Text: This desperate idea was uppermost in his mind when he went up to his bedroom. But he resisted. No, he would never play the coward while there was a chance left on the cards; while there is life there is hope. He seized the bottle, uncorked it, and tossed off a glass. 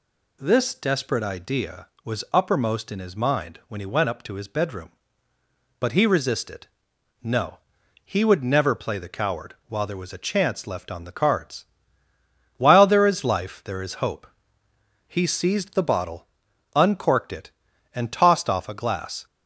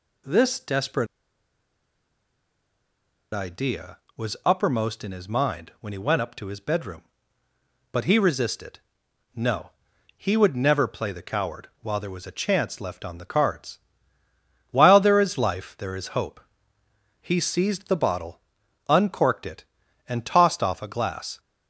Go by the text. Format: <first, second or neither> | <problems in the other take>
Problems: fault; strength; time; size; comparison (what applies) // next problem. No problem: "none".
first | pauses between "desperate" and "idea"; strong; at 1.0 s; 2.2 s long // pauses between "coward" and "while"; slight; at 11.6 s; 0.16 s long; slight in the first